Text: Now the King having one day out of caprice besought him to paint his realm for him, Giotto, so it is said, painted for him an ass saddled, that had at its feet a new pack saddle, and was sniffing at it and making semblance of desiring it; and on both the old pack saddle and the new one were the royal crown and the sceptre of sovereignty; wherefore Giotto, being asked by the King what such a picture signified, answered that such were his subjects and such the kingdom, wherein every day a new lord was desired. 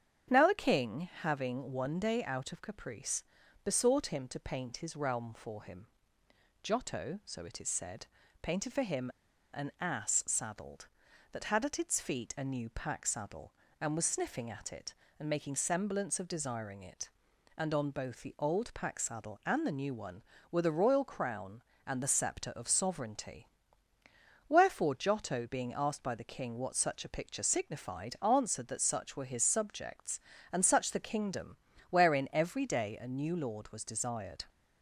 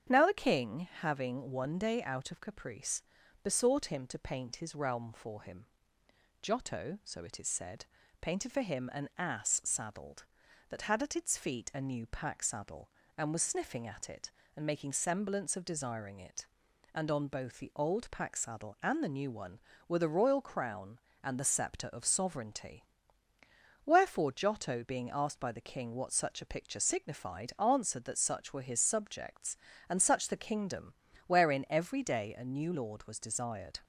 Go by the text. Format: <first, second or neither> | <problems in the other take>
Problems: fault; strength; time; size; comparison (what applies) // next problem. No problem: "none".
second | starts louder than the rest; strong; until 1.4 s; 8.5 dB; strong in the second // pauses between "caprice" and "besought"; at 3.2 s; 0.42 s long; also in the second // pauses between "him" and "an"; noticeable; at 9.0 s; 0.47 s long